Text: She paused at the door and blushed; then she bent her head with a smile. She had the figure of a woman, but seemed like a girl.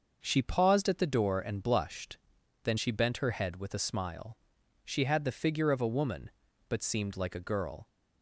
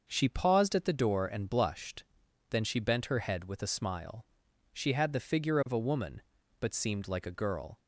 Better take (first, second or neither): neither